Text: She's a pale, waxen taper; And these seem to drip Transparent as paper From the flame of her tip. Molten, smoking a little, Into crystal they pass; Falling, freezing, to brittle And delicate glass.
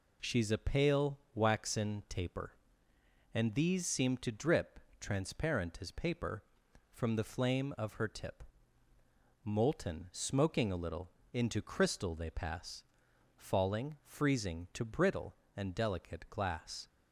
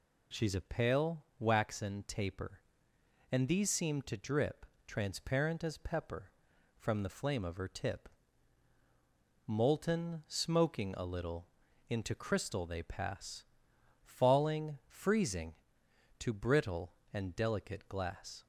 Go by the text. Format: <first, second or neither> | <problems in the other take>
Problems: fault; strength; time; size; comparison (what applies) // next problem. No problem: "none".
first | pauses between "drip" and "Transparent"; slight; at 4.6 s; 0.24 s long; slight in the first // says "pepper" for "paper"; at 5.7 s